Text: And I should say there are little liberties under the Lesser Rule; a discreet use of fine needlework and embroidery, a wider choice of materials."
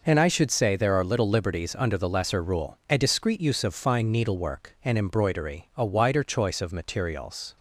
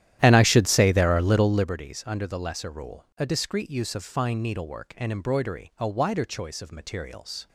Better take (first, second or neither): first